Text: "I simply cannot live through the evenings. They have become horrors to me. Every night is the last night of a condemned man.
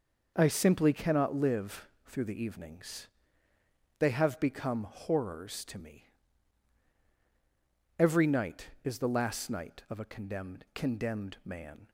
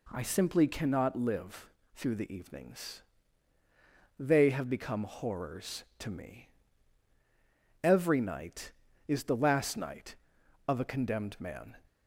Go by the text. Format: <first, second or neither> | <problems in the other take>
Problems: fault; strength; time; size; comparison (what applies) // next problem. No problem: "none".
second | pauses between "live" and "through"; slight; at 1.8 s; 0.18 s long; slight in the second // says "condemned" twice; at 10.7 s